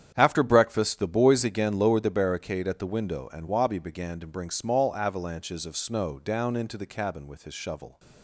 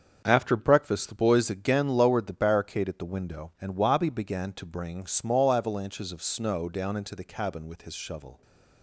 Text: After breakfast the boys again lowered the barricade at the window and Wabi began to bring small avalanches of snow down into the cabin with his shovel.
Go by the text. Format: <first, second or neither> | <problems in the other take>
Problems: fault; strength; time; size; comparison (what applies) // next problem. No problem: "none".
neither | starts louder than the rest; strong; the same in both